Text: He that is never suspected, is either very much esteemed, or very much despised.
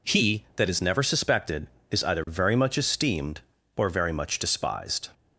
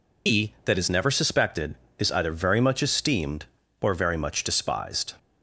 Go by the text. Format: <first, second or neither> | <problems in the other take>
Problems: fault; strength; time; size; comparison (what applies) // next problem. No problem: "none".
first | loses the start of "He"; at 0.2 s; 120 ms